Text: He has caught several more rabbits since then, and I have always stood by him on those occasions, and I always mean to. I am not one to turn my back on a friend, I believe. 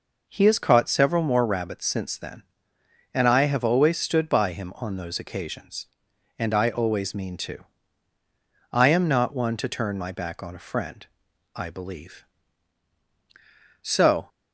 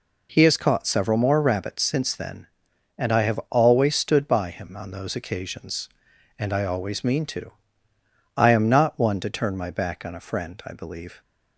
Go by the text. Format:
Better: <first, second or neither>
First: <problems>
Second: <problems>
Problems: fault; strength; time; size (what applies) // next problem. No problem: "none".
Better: second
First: goes on to say "So"; slight; from 13.8 s on; 0.48 s long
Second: none